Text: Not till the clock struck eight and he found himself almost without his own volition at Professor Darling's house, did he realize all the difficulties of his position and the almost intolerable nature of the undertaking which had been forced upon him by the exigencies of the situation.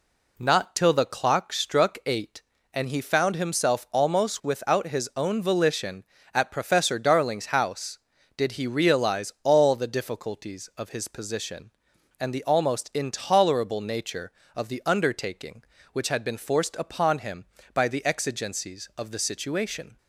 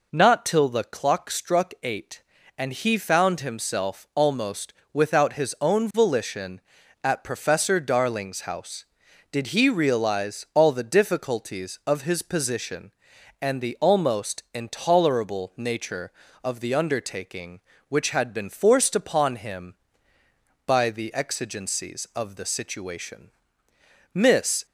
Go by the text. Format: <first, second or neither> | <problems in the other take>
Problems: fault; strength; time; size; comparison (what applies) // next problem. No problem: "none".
first | pauses between "almost" and "without"; slight; at 4.7 s; 0.20 s long // goes on to say "Miss"; from 24.1 s on; 0.52 s long